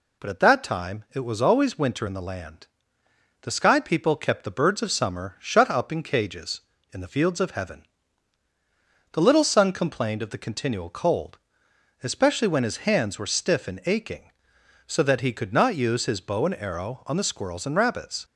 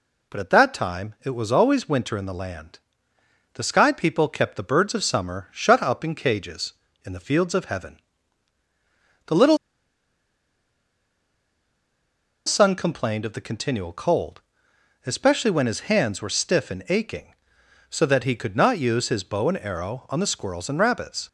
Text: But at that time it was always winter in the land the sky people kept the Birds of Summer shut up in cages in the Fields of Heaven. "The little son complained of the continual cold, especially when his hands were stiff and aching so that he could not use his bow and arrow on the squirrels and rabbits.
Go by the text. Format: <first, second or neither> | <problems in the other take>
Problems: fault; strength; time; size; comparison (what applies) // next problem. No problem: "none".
first | pauses between "land" and "the"; noticeable; at 2.7 s; 0.76 s long; noticeable in the first // pauses between "little" and "son"; strong; at 9.5 s; 2.8 s long